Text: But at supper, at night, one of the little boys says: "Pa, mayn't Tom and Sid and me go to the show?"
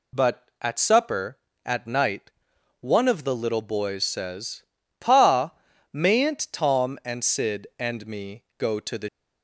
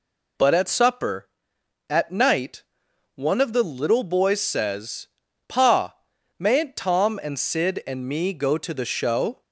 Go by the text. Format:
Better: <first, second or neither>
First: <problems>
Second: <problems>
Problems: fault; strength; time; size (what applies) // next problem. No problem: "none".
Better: second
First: stops before "show"; at 9.0 s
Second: none